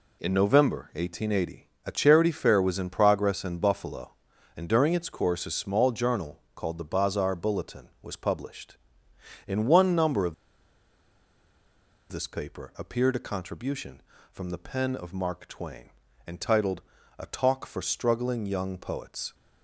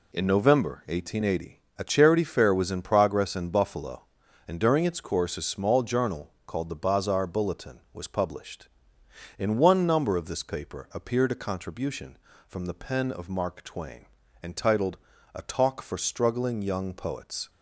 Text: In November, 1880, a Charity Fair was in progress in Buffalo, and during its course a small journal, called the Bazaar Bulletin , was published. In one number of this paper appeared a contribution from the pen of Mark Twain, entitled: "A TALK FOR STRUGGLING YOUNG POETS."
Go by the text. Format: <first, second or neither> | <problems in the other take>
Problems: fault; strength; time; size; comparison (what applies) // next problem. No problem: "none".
second | pauses between "of" and "this"; strong; at 10.3 s; 1.7 s long